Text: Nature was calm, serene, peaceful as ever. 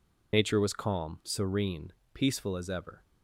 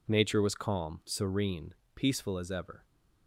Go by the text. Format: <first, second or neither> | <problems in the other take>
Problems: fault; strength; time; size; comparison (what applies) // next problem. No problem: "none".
second | loses the start of "Nature"; at 0.3 s; 70 ms